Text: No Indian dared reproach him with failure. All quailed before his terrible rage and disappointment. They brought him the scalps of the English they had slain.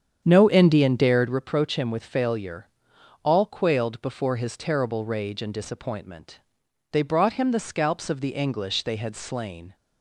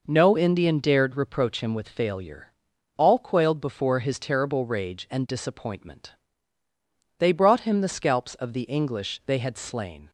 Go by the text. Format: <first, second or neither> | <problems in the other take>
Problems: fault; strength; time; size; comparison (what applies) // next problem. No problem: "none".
second | starts louder than the rest; strong; until 1.5 s; 8 dB